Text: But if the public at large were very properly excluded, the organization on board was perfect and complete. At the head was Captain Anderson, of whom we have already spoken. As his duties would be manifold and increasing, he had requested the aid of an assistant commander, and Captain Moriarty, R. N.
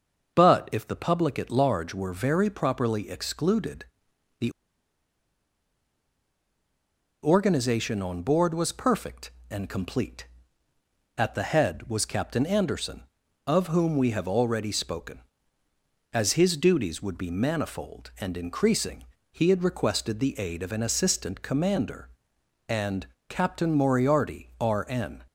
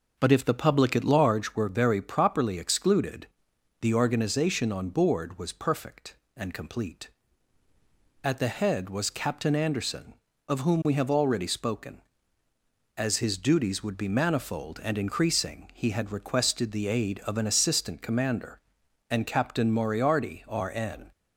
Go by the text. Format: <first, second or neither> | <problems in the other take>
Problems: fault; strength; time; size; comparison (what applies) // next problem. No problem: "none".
second | starts louder than the rest; noticeable; until 1.3 s; 6 dB // pauses between "the" and "organization"; strong; at 4.5 s; 2.7 s long // pauses between "and" and "Captain"; slight; at 23.0 s; 0.22 s long